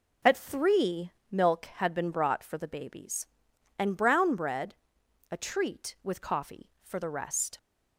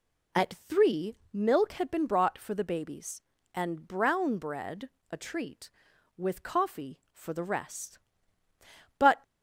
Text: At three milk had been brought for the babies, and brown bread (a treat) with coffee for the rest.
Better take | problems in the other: first | pauses between "three" and "milk"; slight; at 1.1 s; 0.18 s long; slight in the first // goes on to say "But"; slight; from 8.9 s on; 0.26 s long

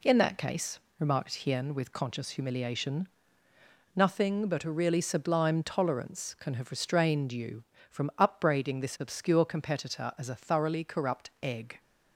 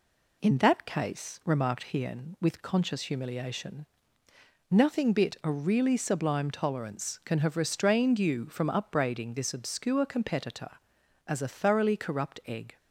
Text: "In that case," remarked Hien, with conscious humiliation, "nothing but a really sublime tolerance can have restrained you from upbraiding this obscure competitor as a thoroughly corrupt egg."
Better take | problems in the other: first | says "bit" for "but"; at 5.1 s

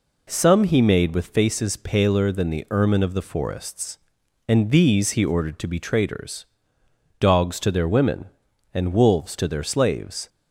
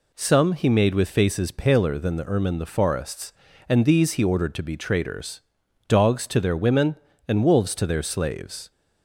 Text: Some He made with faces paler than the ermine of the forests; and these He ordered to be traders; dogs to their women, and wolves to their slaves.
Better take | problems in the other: first | skips "of"; at 2.5 s

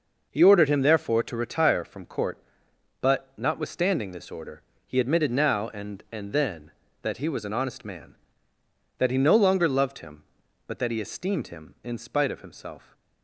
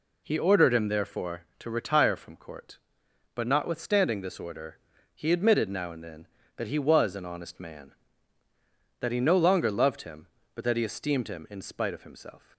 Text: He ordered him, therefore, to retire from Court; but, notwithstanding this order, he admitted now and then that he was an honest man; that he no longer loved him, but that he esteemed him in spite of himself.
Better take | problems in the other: second | says "and" twice; at 6.1 s

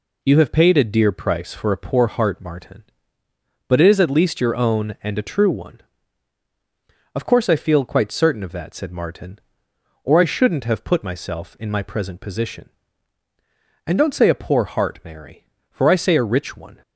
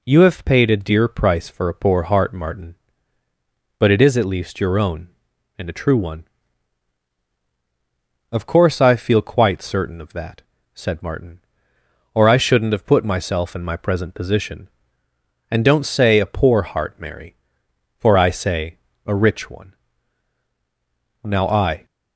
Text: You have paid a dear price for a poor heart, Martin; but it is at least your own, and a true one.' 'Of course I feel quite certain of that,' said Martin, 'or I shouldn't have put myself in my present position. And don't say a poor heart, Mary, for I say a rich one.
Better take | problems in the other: first | pauses between "say" and "a"; slight; at 18.7 s; 0.28 s long // goes on to say "Now I"; noticeable; from 21.2 s on; 0.62 s long

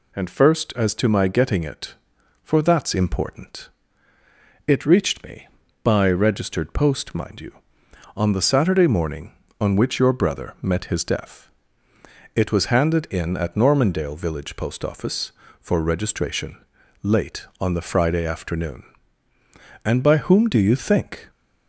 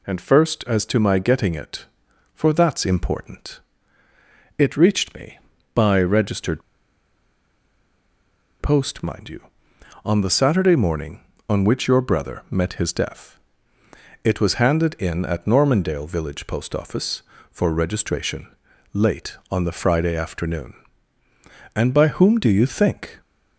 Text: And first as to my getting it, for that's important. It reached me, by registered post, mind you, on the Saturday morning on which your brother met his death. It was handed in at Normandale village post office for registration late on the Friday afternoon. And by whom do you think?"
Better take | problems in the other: first | pauses between "registered" and "post"; strong; at 6.6 s; 2.0 s long // pauses between "registration" and "late"; at 18.4 s; 0.44 s long; also in the first

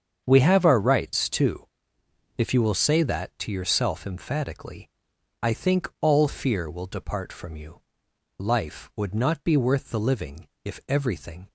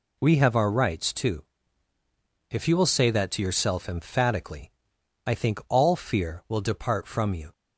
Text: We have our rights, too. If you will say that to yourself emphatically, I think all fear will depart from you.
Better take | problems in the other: second | starts louder than the rest; strong; until 1.2 s; 7.5 dB // goes on to say "Life would not be worth the living if everything"; strong; from 8.3 s on; 3.1 s long

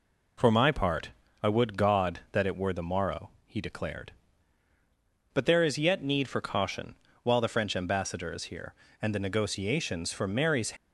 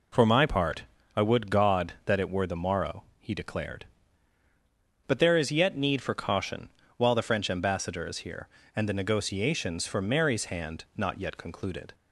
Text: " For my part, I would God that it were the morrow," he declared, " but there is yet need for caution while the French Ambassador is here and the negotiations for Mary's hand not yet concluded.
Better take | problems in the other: second | pauses between "caution" and "while"; slight; at 6.9 s; 0.28 s long; slight in the second // stops before "hand not yet concluded"; at 10.7 s

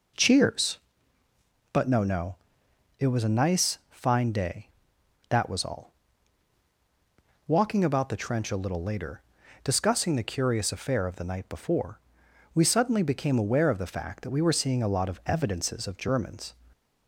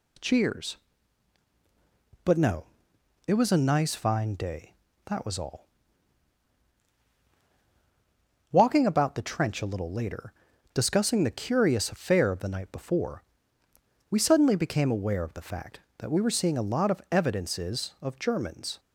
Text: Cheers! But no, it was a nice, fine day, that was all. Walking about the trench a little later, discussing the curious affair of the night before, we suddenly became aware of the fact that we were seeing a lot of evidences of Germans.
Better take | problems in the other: second | says "no" twice; at 2.0 s

